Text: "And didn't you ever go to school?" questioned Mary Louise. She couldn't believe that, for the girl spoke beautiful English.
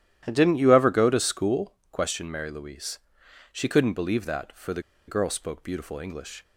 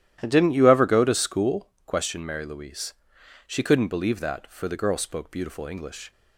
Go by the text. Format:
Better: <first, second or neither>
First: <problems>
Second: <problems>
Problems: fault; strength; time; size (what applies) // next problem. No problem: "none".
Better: second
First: starts louder than the rest; strong; until 1.2 s; 11.5 dB // pauses between "the" and "girl"; slight; at 4.8 s; 0.25 s long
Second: starts louder than the rest; strong; until 1.2 s; 12 dB